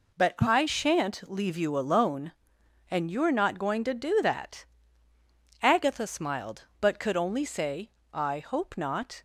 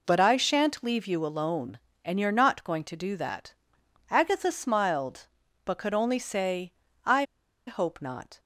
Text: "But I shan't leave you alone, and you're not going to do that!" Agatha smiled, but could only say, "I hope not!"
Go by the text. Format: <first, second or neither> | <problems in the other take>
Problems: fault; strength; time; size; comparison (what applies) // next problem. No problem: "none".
first | pauses between "I" and "hope"; at 7.2 s; 0.43 s long